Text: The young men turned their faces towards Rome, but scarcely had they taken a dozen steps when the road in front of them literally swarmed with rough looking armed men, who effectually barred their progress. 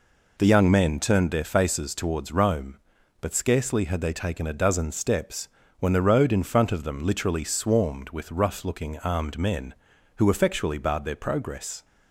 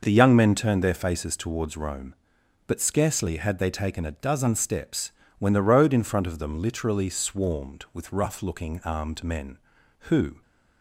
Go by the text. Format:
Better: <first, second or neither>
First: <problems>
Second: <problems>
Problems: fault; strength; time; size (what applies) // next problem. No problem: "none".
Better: first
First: pauses between "steps" and "when"; slight; at 5.4 s; 0.32 s long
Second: pauses between "steps" and "when"; slight; at 5.1 s; 0.26 s long // stops before "effectually barred their progress"; at 10.4 s